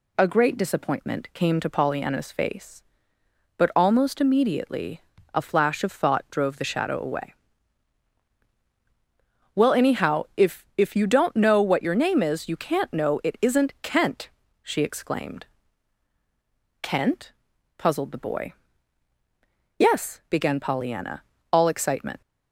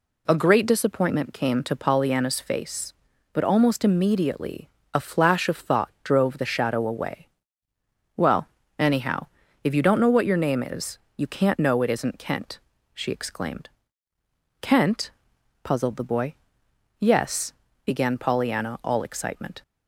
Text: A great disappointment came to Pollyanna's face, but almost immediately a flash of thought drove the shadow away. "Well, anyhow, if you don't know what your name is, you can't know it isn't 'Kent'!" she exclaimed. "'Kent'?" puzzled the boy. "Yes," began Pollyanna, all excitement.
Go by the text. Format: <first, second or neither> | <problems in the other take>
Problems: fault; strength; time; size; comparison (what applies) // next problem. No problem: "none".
second | pauses between "immediately" and "a"; slight; at 5.0 s; 0.32 s long; slight in the second // says "if" twice; at 10.7 s